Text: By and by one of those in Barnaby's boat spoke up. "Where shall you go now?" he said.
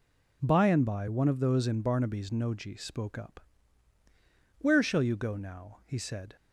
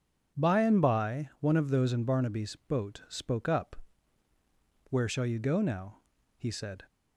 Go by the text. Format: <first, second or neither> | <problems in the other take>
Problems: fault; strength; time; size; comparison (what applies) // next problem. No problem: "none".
second | says "noji" for "boat"; at 2.2 s